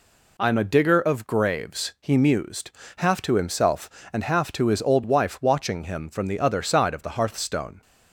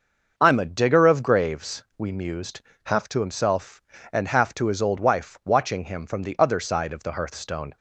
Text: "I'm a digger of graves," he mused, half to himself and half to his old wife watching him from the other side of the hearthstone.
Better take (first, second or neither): first